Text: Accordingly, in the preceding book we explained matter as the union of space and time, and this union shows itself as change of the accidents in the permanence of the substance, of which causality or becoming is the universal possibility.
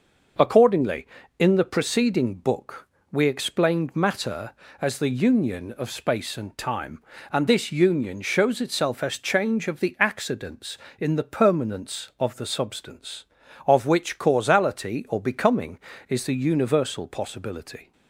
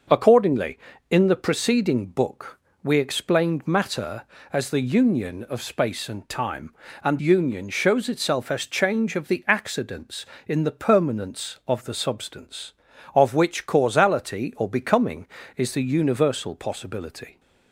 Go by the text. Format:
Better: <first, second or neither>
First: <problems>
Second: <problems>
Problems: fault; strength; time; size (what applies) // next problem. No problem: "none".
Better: first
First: pauses between "book" and "we"; slight; at 2.8 s; 0.24 s long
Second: starts louder than the rest; noticeable; until 1.4 s; 6 dB // pauses between "book" and "we"; slight; at 2.5 s; 0.24 s long // skips "this"; at 7.1 s